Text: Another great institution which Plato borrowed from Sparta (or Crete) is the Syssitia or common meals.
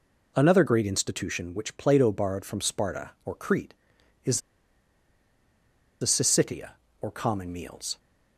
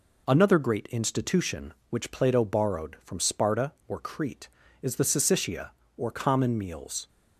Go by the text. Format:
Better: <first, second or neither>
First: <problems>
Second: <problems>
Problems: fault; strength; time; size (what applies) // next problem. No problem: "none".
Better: second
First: pauses between "is" and "the"; strong; at 4.3 s; 1.6 s long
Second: none